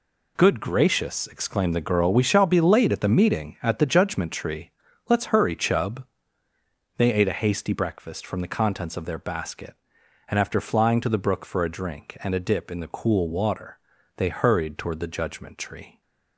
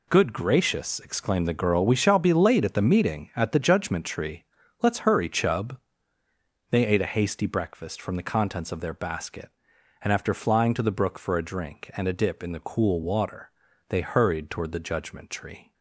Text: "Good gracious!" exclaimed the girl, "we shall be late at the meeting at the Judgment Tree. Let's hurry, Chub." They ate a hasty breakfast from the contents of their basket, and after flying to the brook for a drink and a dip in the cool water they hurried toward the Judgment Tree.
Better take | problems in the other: neither | pauses between "water" and "they"; the same in both

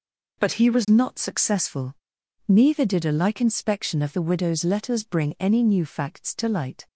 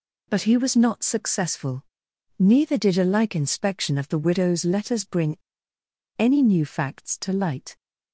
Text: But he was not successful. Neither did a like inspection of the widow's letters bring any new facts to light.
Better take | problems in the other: first | pauses between "bring" and "any"; noticeable; at 5.3 s; 0.80 s long

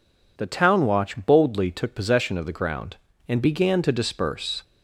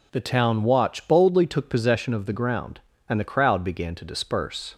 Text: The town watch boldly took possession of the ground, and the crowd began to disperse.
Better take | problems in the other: second | skips "the crowd"; at 3.4 s

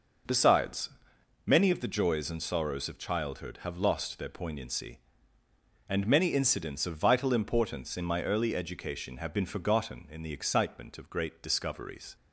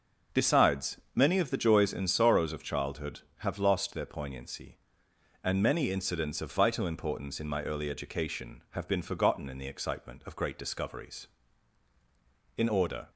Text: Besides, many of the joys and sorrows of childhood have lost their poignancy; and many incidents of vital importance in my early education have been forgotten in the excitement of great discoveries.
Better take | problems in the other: first | starts louder than the rest; noticeable; until 1.4 s; 6 dB // goes on to say "In order"; from 12.5 s on; 0.50 s long

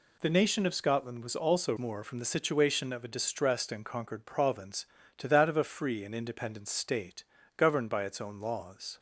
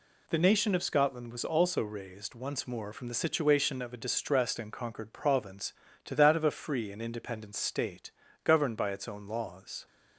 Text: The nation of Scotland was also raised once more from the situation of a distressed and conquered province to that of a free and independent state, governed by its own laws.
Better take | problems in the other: second | skips "raised once"; at 1.7 s

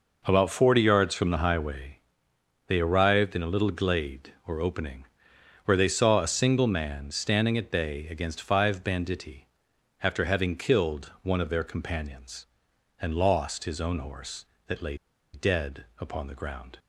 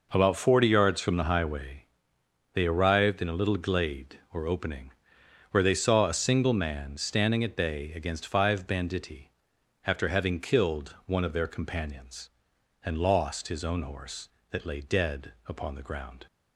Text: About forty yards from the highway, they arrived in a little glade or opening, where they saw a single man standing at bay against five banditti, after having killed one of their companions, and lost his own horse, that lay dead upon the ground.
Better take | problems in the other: second | pauses between "lay" and "dead"; at 14.9 s; 0.38 s long // pauses between "dead" and "upon"; slight; at 15.8 s; 0.16 s long; slight in the second

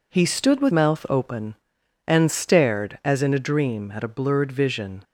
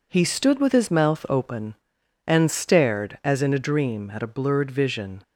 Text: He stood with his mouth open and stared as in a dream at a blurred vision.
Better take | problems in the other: second | skips "his"; at 0.7 s

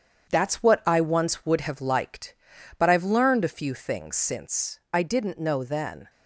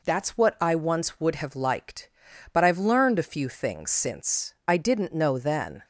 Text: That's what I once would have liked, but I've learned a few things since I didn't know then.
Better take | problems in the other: second | gets quieter; throughout; 6.5 dB

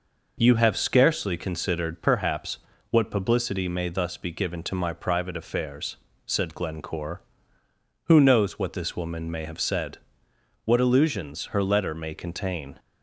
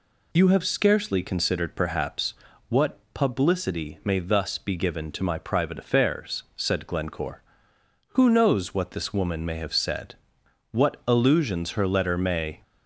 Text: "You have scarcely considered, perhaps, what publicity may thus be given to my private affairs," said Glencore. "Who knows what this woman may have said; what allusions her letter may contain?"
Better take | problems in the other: first | stops before "contain"; at 12.6 s

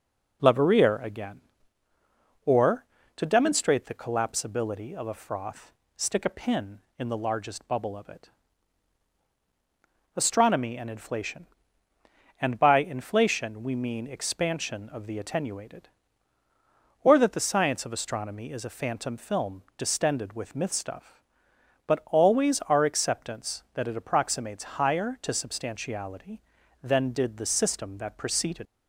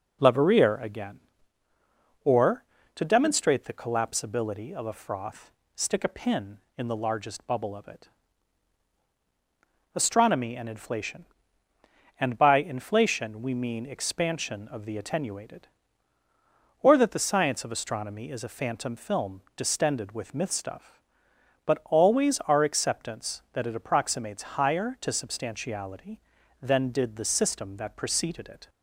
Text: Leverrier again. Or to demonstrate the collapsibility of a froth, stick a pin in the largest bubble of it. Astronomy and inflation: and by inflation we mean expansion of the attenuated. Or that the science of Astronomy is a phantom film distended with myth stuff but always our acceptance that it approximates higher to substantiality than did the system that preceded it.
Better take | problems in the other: second | pauses between "film" and "distended"; slight; at 19.6 s; 0.16 s long; slight in the second // stops before "it"; at 28.6 s

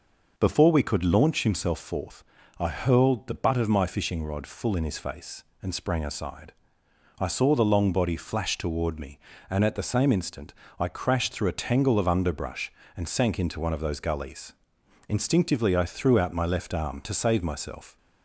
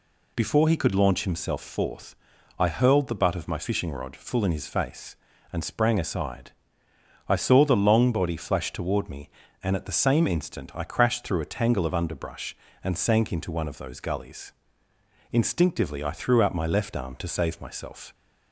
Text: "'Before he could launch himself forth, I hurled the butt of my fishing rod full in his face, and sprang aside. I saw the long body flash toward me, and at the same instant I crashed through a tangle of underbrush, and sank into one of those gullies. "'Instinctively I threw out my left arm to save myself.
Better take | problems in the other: second | says "we" for "he"; at 0.6 s // pauses between "instant" and "I"; slight; at 10.5 s; 0.24 s long

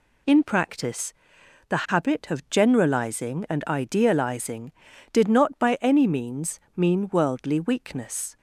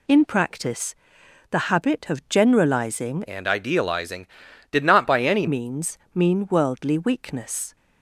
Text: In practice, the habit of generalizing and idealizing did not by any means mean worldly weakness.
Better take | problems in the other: first | changes voice from "and" to "any"; from 3.2 to 5.4 s; 2.2 s long // pauses between "means" and "mean"; slight; at 5.9 s; 0.18 s long; slight in the first

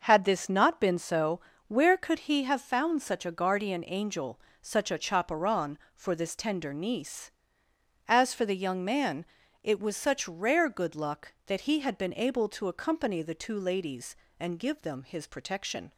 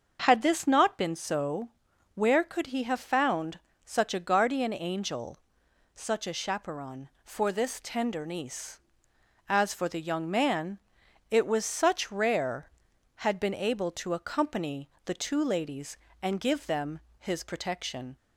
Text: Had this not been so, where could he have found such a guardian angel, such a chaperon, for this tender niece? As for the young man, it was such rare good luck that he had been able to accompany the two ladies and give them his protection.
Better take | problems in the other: first | starts louder than the rest; until 1.2 s; 6.5 dB // pauses between "found" and "such"; slight; at 3.5 s; 0.28 s long // skips "good luck that he"; at 12.9 s // pauses between "accompany" and "the"; slight; at 14.9 s; 0.16 s long // pauses between "them" and "his"; slight; at 16.9 s; 0.20 s long

